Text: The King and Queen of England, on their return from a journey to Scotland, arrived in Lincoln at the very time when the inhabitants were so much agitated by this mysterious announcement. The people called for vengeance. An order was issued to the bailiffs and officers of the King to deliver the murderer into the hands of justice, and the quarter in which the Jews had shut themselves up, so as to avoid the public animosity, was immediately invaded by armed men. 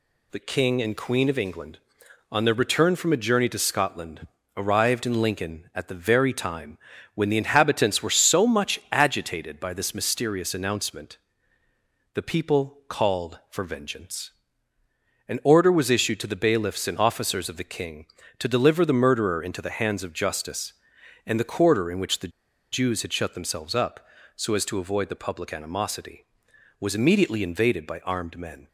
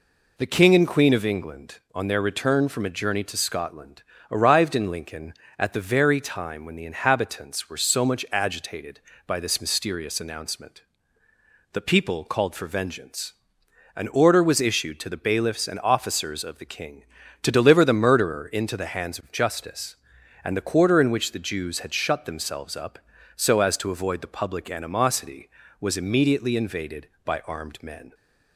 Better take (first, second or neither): second